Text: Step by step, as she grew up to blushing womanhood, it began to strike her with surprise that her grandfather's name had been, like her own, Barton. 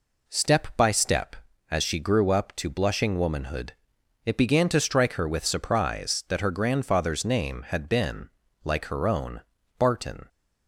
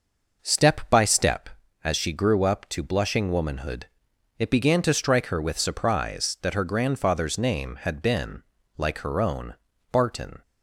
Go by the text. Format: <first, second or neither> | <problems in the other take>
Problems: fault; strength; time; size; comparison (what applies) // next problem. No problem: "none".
first | starts louder than the rest; noticeable; until 1.4 s; 5.5 dB